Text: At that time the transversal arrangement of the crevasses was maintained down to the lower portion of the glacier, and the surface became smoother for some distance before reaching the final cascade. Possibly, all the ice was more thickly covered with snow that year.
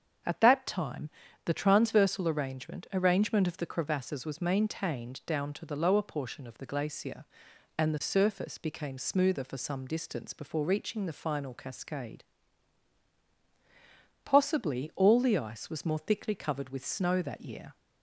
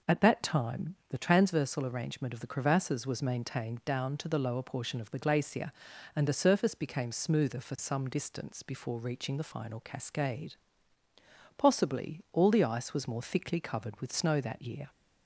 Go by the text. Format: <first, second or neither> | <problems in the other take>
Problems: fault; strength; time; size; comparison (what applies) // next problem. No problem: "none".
second | starts louder than the rest; strong; until 1.6 s; 7 dB // pauses between "time" and "the"; slight; at 1.1 s; 0.34 s long // says "arrangement" twice; at 2.9 s